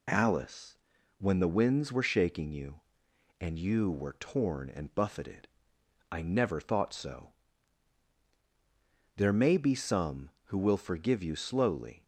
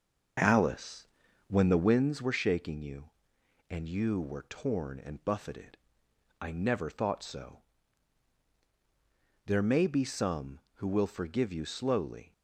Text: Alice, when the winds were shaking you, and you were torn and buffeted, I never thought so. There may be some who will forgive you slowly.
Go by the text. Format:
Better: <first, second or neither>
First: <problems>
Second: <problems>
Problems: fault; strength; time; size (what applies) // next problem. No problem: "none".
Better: first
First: none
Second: starts louder than the rest; until 2.1 s; 6 dB